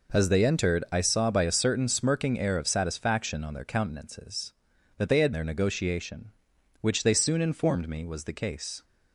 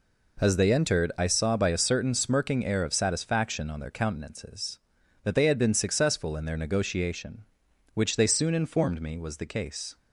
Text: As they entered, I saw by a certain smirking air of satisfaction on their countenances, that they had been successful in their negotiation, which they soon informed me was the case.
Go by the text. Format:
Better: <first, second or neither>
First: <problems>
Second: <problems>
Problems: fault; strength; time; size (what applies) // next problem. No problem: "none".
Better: second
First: skips "been successful in"; at 5.3 s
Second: none